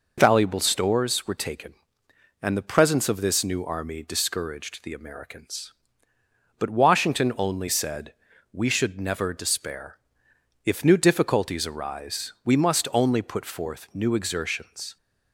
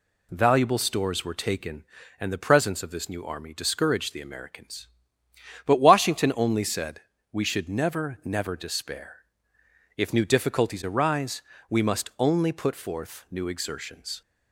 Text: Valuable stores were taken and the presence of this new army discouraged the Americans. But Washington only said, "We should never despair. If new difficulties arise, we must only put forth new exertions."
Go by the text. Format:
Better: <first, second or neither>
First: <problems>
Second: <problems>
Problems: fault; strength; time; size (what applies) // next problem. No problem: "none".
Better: first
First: none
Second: says "never" twice; at 8.2 s